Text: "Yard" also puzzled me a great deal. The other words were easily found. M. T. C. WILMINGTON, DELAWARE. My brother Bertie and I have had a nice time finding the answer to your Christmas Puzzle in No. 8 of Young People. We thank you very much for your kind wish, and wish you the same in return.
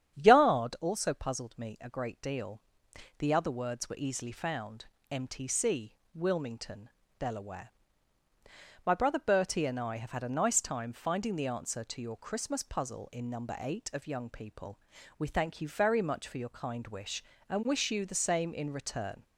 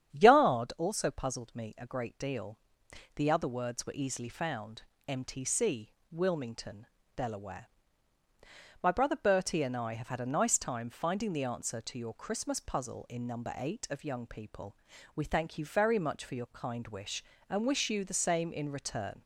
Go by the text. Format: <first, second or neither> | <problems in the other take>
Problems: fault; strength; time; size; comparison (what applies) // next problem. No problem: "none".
neither | starts louder than the rest; strong; the same in both // pauses between "C" and "WILMINGTON"; slight; the same in both